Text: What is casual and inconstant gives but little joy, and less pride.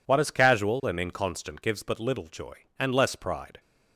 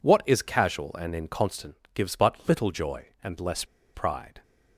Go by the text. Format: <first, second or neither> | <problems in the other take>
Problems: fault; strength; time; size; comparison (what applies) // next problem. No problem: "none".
first | pauses between "inconstant" and "gives"; slight; at 1.7 s; 0.18 s long // pauses between "less" and "pride"; slight; at 3.6 s; 0.30 s long